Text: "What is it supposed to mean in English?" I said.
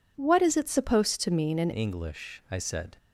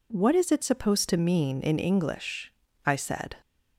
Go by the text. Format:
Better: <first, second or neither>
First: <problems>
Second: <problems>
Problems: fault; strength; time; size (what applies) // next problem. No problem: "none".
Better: second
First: changes voice at "English"; from 1.7 s on; 1.2 s long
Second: none